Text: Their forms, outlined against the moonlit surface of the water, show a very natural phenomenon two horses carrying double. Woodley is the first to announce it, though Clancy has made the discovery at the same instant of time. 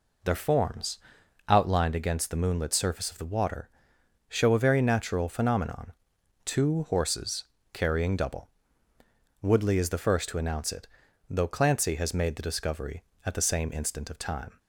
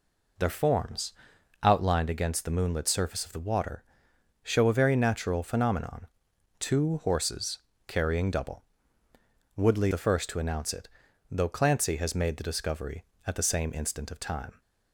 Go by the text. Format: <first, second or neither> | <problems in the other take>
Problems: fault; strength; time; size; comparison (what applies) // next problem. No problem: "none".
first | pauses between "phenomenon" and "two"; noticeable; at 6.0 s; 0.52 s long; noticeable in the first // pauses between "horses" and "carrying"; slight; at 7.5 s; 0.28 s long; slight in the first // skips "is"; at 9.9 s